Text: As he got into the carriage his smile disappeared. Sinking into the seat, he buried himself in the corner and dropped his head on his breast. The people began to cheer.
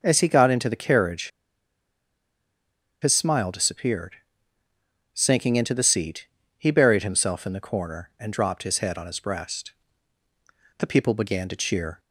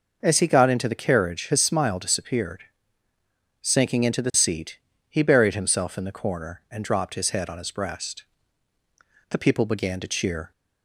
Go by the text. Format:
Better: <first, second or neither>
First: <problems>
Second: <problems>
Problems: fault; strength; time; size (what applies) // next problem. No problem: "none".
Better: second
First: pauses between "carriage" and "his"; strong; at 1.2 s; 1.7 s long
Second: none